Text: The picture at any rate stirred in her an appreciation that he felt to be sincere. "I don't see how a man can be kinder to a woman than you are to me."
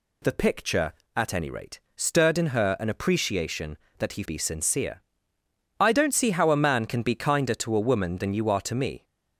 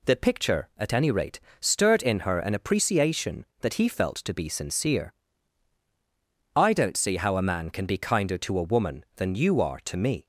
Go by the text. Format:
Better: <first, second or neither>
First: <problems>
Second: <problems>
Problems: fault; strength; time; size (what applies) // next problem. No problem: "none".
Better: second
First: pauses between "rate" and "stirred"; slight; at 1.8 s; 0.16 s long // skips "felt to"; at 4.2 s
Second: pauses between "rate" and "stirred"; slight; at 1.3 s; 0.22 s long